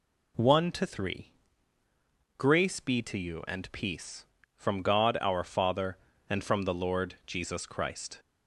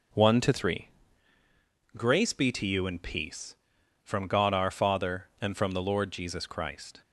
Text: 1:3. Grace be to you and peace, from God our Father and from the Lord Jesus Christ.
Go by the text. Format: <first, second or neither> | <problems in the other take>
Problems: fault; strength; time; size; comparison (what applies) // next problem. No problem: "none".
first | gets quieter; throughout; 6.5 dB